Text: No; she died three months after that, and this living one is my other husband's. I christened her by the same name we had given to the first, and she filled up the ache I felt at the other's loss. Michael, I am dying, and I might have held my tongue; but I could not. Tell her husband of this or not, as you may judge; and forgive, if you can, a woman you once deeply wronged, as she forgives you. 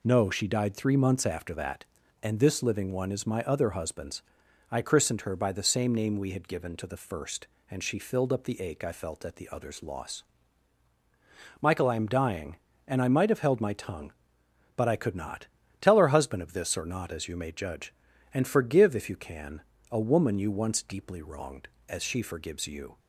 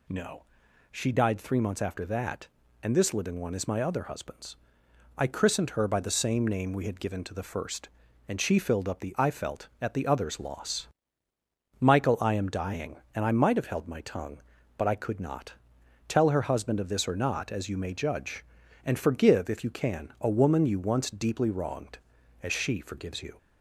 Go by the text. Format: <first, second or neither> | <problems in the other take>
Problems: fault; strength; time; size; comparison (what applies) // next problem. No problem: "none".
first | skips "ache"; at 9.1 s